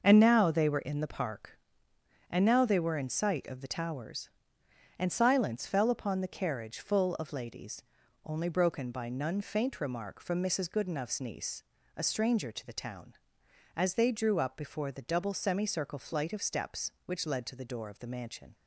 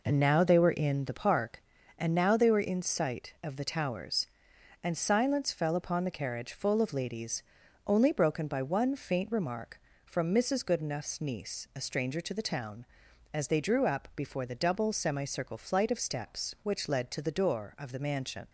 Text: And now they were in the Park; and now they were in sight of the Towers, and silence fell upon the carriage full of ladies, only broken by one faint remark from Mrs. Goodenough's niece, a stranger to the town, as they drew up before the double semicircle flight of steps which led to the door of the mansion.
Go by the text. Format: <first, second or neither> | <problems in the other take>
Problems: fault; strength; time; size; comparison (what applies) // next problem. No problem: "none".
second | starts louder than the rest; noticeable; until 1.0 s; 6 dB // says "none" for "one"; at 9.0 s